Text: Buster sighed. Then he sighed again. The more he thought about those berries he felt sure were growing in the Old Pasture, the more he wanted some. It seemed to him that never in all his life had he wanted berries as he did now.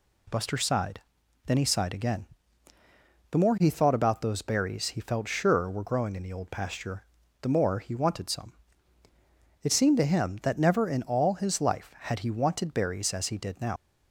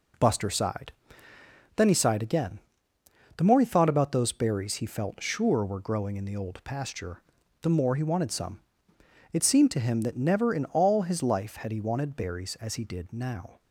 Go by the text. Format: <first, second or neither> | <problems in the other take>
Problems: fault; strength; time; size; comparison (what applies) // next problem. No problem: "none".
second | leaves "now" unfinished; at 13.7 s; 80 ms